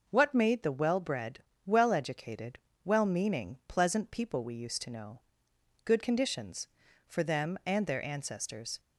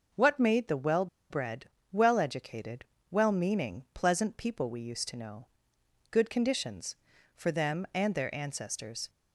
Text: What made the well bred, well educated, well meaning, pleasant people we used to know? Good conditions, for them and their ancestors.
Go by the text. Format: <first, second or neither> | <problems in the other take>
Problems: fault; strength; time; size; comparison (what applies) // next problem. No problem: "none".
first | pauses between "well" and "bred"; slight; at 1.0 s; 0.24 s long